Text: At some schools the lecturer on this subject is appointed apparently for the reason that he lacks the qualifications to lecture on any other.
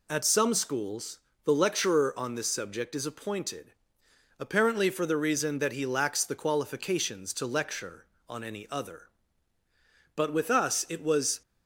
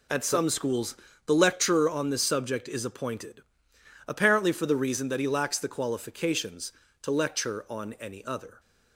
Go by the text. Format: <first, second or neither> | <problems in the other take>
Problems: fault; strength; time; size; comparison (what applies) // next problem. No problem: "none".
second | pauses between "schools" and "the"; slight; at 1.1 s; 0.26 s long; slight in the second // pauses between "appointed" and "apparently"; noticeable; at 3.7 s; 0.66 s long; noticeable in the second // goes on to say "But with us it was"; noticeable; from 10.1 s on; 1.2 s long